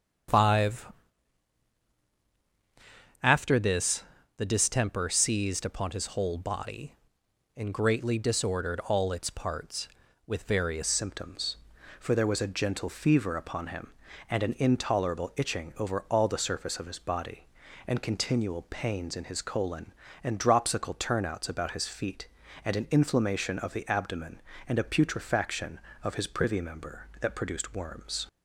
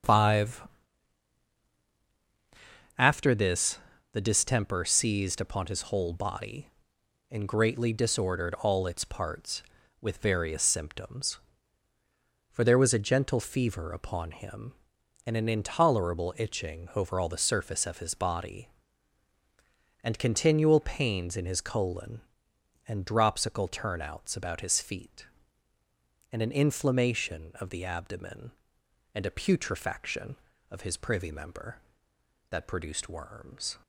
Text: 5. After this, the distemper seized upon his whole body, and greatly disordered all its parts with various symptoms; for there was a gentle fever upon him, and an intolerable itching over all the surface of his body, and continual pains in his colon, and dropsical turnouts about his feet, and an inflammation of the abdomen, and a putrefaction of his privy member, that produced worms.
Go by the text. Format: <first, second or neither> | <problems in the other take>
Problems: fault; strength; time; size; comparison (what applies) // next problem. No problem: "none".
second | starts louder than the rest; strong; until 3.6 s; 8 dB; also in the second // changes voice at "symptoms"; from 10.8 s on; 17.4 s long